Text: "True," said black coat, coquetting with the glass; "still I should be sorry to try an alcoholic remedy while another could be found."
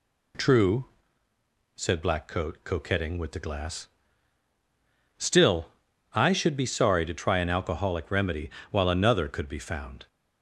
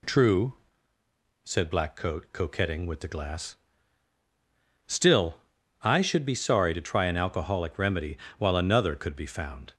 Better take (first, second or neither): neither